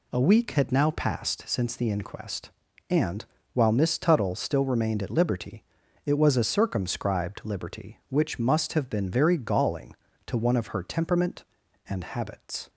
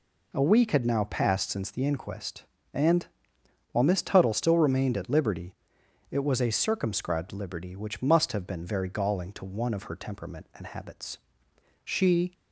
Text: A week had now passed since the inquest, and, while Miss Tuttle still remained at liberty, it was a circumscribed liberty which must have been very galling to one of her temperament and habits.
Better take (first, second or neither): first